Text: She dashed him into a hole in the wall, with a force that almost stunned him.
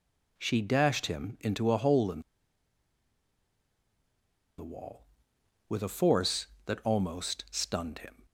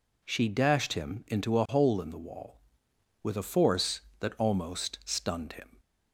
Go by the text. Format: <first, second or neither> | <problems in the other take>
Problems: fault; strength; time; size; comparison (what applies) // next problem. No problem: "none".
second | pauses between "in" and "the"; strong; at 2.1 s; 2.3 s long